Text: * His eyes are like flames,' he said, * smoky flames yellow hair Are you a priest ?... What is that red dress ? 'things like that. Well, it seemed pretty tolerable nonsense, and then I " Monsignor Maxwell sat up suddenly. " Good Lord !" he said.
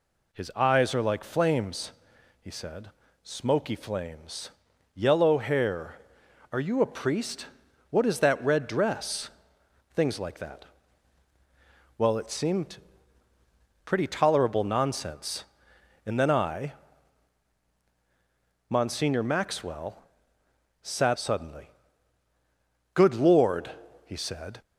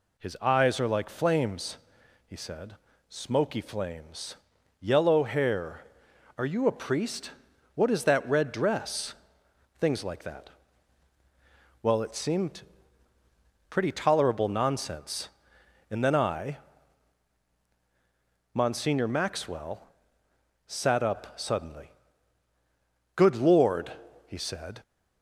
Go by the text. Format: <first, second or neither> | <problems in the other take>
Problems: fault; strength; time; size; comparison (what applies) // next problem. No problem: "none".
second | pauses between "flames" and "yellow"; noticeable; at 4.4 s; 0.46 s long; noticeable in the second // pauses between "seemed" and "pretty"; at 12.7 s; 1.0 s long; also in the second // pauses between "Maxwell" and "sat"; noticeable; at 20.0 s; 0.80 s long; noticeable in the second // skips "up"; at 21.1 s